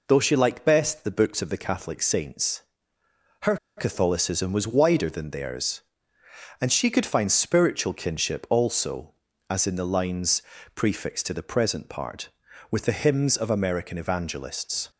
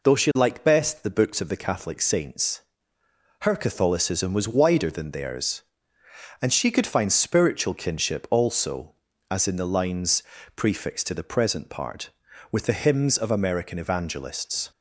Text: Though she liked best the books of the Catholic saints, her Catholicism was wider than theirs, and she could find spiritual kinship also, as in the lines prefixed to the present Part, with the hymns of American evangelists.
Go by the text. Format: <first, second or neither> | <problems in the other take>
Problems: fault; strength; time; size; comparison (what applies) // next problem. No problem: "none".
second | pauses between "her" and "Catholicism"; slight; at 3.5 s; 0.21 s long // pauses between "lines" and "prefixed"; slight; at 10.4 s; 0.32 s long; slight in the second